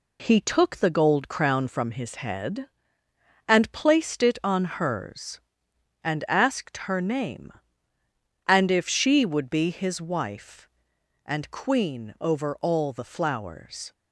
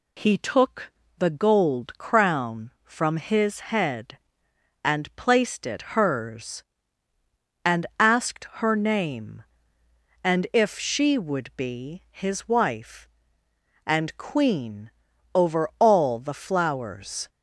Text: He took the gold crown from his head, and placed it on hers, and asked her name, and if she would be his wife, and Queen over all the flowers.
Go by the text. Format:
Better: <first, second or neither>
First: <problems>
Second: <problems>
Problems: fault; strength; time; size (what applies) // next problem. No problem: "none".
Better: first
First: none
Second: pauses between "took" and "the"; slight; at 0.8 s; 0.30 s long // skips "on"; at 5.9 s // pauses between "Queen" and "over"; noticeable; at 14.8 s; 0.46 s long